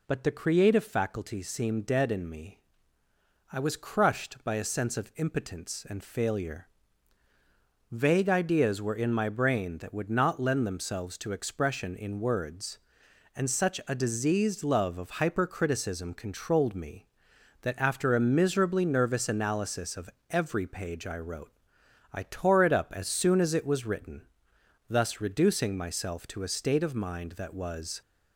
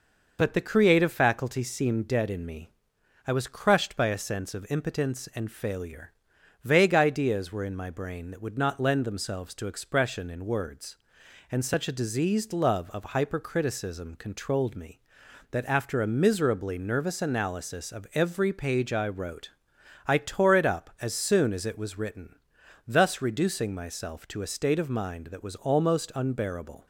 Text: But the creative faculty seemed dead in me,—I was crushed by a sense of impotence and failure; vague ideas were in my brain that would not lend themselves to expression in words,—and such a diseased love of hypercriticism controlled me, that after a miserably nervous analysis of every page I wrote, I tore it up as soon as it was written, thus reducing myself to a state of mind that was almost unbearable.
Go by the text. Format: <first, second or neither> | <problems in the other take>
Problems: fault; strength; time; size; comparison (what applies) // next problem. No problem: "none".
second | pauses between "of" and "every"; slight; at 20.0 s; 0.20 s long // stops before "almost unbearable"; at 28.0 s